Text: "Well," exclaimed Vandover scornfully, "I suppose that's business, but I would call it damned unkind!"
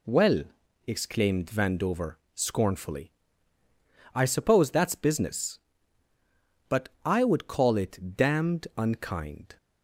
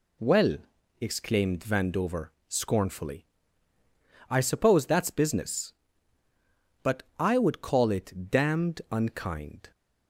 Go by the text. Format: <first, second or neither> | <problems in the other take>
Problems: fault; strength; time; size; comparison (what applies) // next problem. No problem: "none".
neither | pauses between "Vandover" and "scornfully"; slight; the same in both // pauses between "but" and "I"; slight; the same in both